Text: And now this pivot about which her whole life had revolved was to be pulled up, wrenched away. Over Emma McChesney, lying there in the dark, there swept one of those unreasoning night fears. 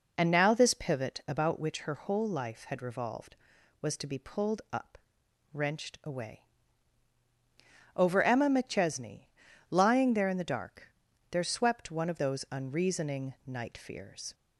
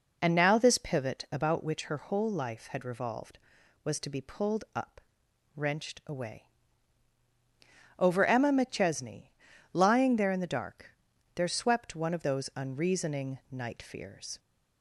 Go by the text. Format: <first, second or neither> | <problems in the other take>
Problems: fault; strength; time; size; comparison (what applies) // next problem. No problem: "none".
neither | none